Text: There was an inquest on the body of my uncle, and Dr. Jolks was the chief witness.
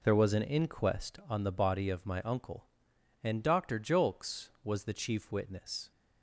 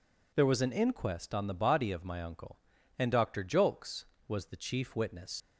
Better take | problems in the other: first | leaves "witness" unfinished; at 5.4 s; 105 ms

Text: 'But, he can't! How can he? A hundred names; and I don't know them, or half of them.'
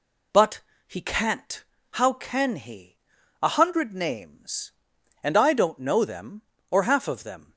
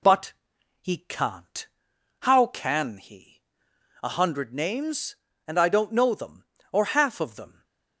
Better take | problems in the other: neither | none

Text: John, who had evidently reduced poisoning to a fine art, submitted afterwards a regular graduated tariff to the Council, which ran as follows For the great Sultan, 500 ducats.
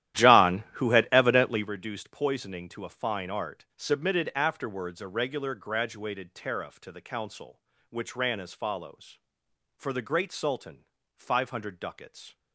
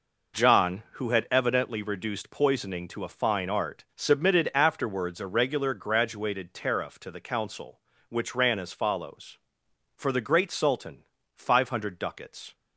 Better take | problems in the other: second | starts louder than the rest; strong; until 1.7 s; 12.5 dB

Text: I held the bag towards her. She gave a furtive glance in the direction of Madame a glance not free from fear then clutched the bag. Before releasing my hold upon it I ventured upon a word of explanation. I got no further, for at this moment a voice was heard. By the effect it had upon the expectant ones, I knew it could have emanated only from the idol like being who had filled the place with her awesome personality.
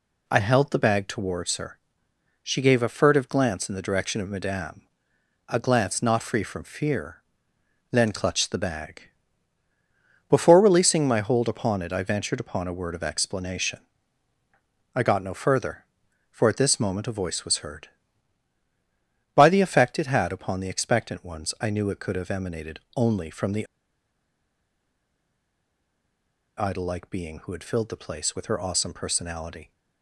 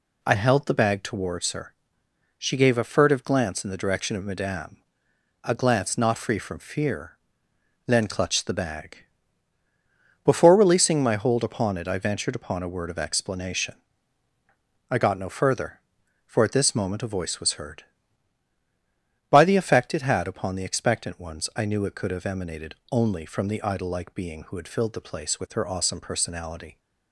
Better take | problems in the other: second | pauses between "Madame" and "a"; noticeable; at 4.8 s; 0.66 s long; noticeable in the second // pauses between "fear" and "then"; noticeable; at 7.2 s; 0.70 s long; noticeable in the second // pauses between "emanated" and "only"; slight; at 22.8 s; 0.16 s long; slight in the second // pauses between "the" and "idol"; strong; at 23.6 s; 2.9 s long

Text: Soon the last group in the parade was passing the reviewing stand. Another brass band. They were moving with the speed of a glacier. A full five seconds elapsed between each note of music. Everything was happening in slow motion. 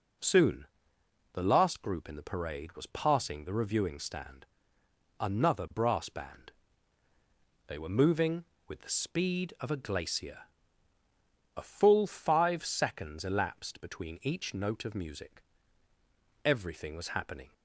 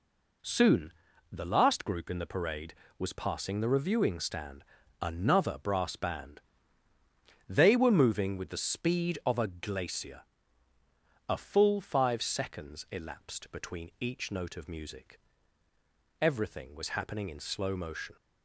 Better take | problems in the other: second | pauses between "Soon" and "the"; noticeable; at 0.6 s; 0.66 s long; also in the second // stops before "in slow motion"; at 17.5 s

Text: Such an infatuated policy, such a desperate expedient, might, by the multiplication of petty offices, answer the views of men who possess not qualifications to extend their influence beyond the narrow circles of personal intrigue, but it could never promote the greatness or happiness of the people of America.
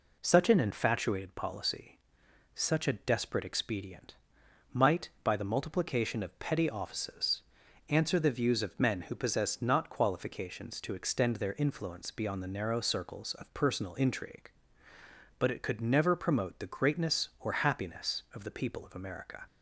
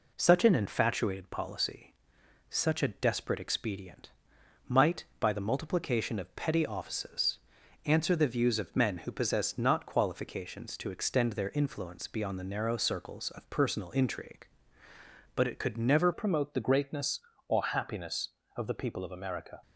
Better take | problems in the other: first | changes voice at "promote"; from 16.1 s on; 3.5 s long

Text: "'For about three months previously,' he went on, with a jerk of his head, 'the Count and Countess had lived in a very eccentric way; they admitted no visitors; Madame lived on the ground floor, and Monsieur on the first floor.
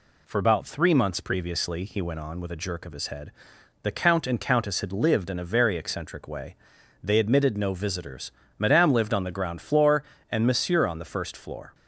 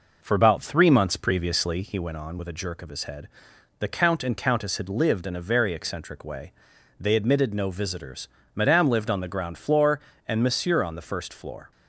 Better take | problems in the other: first | starts louder than the rest; noticeable; until 2.0 s; 5 dB

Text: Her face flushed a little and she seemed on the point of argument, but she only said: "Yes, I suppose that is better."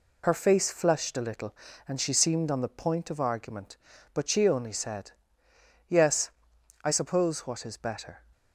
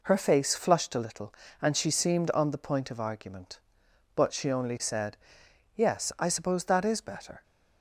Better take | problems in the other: second | says "what" for "that"; at 7.4 s

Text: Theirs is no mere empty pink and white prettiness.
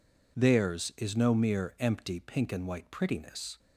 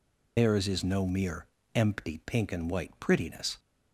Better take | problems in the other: first | loses the start of "Theirs"; at 0.3 s; 140 ms // pauses between "mere" and "empty"; slight; at 1.4 s; 0.28 s long

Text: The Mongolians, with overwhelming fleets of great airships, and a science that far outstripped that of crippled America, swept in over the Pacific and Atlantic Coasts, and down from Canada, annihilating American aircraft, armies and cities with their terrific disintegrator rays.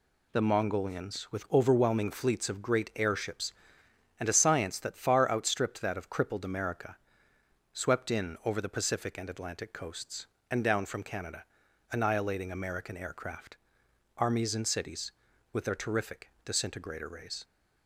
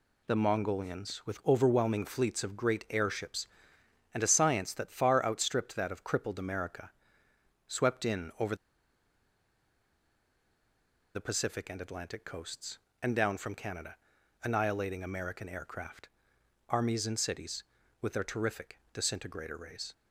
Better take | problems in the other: first | pauses between "over" and "the"; strong; at 8.5 s; 2.5 s long // pauses between "terrific" and "disintegrator"; slight; at 18.7 s; 0.16 s long; slight in the first

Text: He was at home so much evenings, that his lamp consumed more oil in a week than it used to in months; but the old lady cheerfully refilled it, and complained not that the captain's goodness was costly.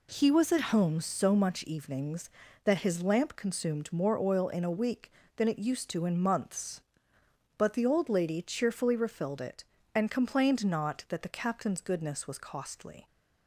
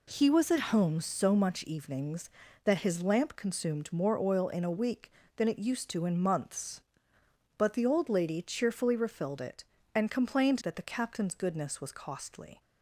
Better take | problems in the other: first | skips "not"; at 10.6 s

